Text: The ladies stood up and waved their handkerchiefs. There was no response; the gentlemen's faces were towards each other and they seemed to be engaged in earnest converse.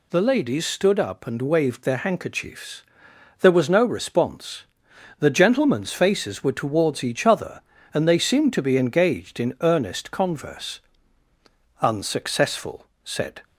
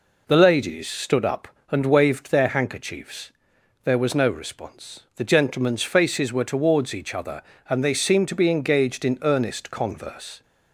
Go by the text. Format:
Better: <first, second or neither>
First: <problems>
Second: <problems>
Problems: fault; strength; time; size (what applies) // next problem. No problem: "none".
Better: second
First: goes on to say "Unsuccessful said"; from 11.7 s on; 1.6 s long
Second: none